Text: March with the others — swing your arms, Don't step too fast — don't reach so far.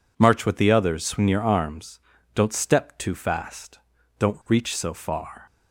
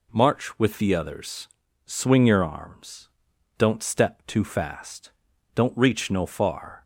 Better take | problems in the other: first | says "no" for "so"; at 6.1 s

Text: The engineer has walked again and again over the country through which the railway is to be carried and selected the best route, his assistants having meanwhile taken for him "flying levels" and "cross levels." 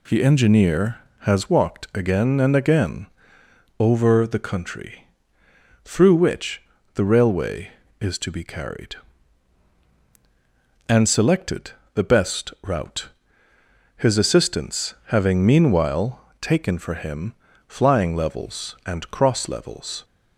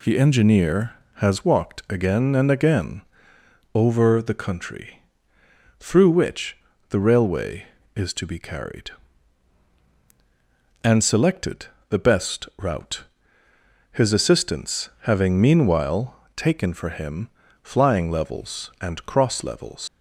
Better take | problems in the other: first | pauses between "again" and "over"; noticeable; at 3.0 s; 0.74 s long; noticeable in the first // pauses between "country" and "through"; noticeable; at 5.0 s; 0.76 s long; noticeable in the first // pauses between "which" and "the"; slight; at 6.5 s; 0.32 s long; slight in the first // pauses between "selected" and "the"; slight; at 11.6 s; 0.22 s long; slight in the first // pauses between "meanwhile" and "taken"; slight; at 16.1 s; 0.20 s long; slight in the first // pauses between "him" and "flying"; slight; at 17.2 s; 0.32 s long; slight in the first // leaves "levels" unfinished; at 19.8 s; 115 ms

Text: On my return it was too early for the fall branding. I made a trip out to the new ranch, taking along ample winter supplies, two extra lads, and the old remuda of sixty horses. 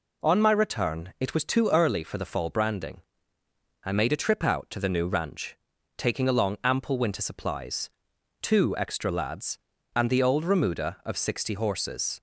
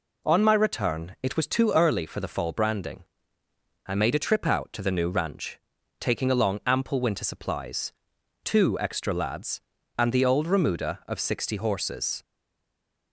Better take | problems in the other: first | stays silent after the last word; slight; from 12.2 s on; 0.9 s long

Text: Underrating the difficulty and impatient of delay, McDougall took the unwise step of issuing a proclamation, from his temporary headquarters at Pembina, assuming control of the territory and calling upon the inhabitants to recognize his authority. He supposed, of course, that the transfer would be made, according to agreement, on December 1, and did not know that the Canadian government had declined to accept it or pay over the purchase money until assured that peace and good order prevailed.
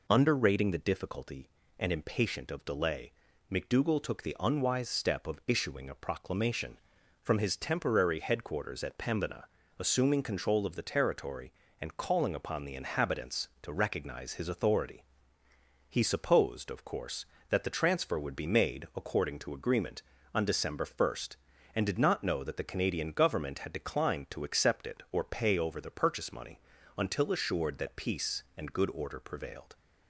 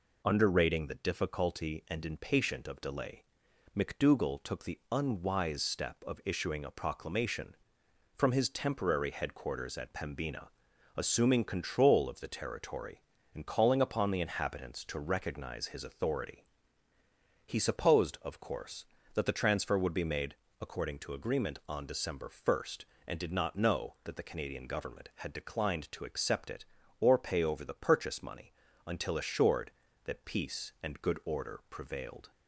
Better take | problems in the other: neither | pauses between "money" and "until"; slight; the same in both

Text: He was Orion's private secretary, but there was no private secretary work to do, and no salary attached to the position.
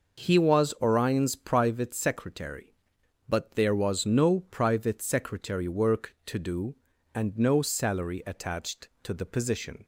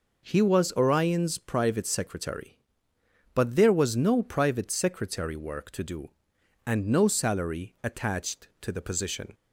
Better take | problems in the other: neither | none

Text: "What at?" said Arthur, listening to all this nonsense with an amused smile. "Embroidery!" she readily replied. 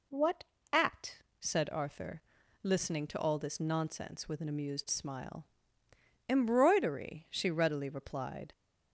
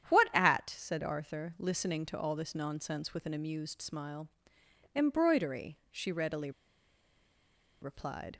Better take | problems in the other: first | starts louder than the rest; strong; until 1.1 s; 9.5 dB // pauses between "readily" and "replied"; strong; at 6.5 s; 1.3 s long

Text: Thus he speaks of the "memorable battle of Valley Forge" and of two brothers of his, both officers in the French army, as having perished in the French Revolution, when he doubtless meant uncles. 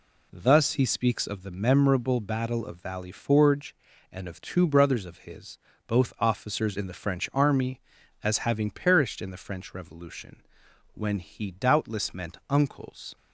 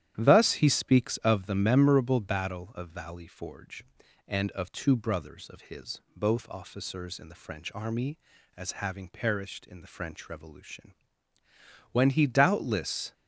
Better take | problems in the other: first | starts louder than the rest; strong; until 1.1 s; 11.5 dB // stops before "meant uncles"; at 13.1 s

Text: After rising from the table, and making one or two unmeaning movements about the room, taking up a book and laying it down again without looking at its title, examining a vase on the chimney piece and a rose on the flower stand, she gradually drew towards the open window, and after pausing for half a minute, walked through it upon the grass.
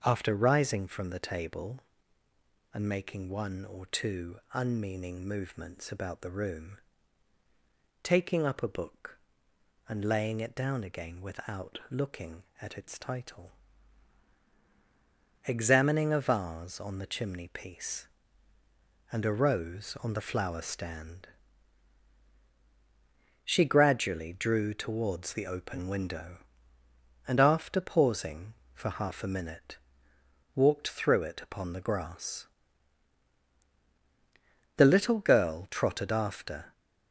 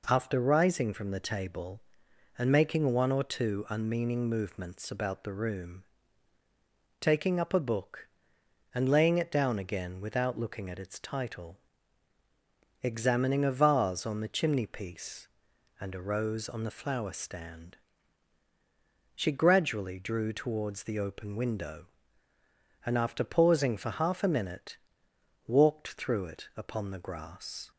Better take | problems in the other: second | starts louder than the rest; until 1.0 s; 7 dB // pauses between "two" and "unmeaning"; slight; at 4.3 s; 0.18 s long // goes on to say "The little girl trotted after"; strong; from 34.7 s on; 1.9 s long

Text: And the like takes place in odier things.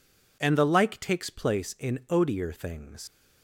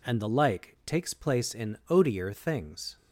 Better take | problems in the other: second | leaves "things" unfinished; at 3.0 s; 90 ms

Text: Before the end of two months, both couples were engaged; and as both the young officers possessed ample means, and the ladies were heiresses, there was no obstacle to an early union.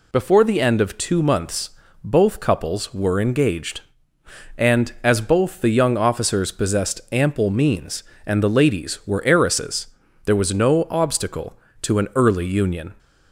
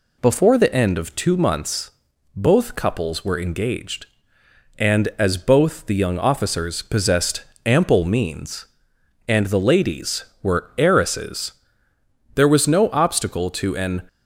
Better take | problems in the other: first | pauses between "possessed" and "ample"; slight; at 7.4 s; 0.20 s long // stops before "early union"; at 14.0 s

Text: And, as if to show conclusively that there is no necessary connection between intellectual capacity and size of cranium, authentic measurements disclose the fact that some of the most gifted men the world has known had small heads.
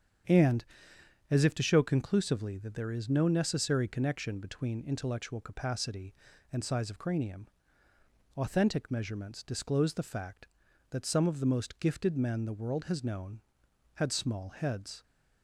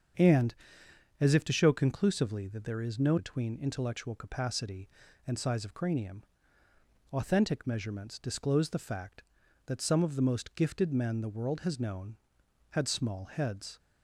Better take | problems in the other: first | starts louder than the rest; strong; until 1.8 s; 7.5 dB; strong in the first // skips "necessary connection"; at 3.1 s

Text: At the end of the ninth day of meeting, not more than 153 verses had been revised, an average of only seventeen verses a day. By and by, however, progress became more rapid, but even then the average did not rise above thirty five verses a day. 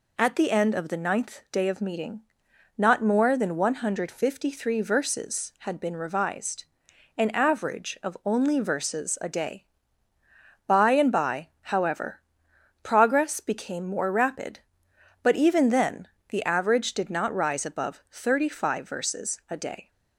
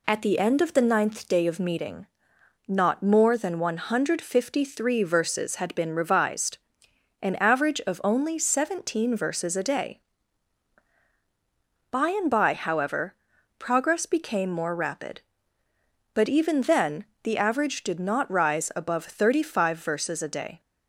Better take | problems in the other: second | skips "seventeen"; at 8.6 s // pauses between "then" and "the"; slight; at 16.0 s; 0.22 s long; slight in the second

